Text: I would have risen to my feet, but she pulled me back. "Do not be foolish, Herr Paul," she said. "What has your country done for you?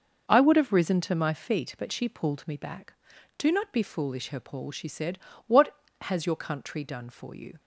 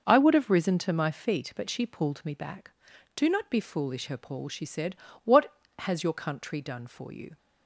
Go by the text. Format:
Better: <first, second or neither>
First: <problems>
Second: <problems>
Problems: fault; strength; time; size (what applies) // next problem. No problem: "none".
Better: neither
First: none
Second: none